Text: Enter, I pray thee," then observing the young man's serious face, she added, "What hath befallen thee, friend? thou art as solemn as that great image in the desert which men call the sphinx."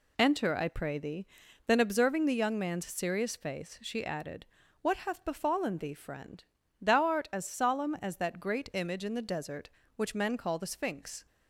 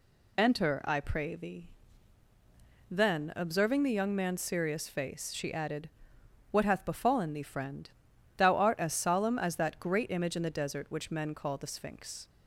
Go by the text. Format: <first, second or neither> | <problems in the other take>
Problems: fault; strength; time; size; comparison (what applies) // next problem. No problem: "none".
neither | none